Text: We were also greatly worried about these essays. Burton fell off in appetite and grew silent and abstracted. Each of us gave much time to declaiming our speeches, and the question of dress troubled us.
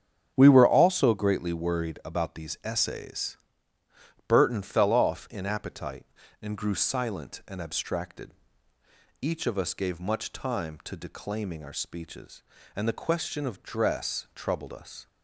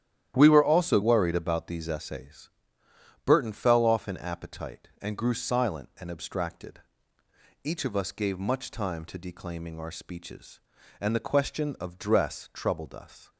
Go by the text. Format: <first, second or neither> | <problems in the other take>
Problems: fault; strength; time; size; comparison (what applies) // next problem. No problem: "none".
first | starts louder than the rest; strong; until 1.3 s; 11 dB; strong in the first // skips "greatly"; at 1.0 s